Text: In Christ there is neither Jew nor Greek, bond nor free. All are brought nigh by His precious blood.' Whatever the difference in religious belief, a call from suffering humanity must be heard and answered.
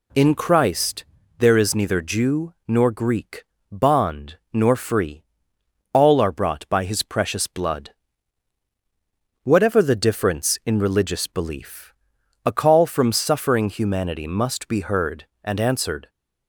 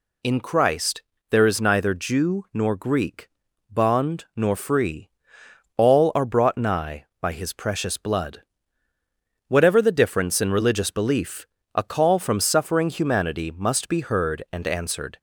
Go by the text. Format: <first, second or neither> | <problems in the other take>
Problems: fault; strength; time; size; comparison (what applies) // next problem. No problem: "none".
second | pauses between "Christ" and "there"; slight; at 1.0 s; 0.34 s long; slight in the second // skips "nigh"; at 6.6 s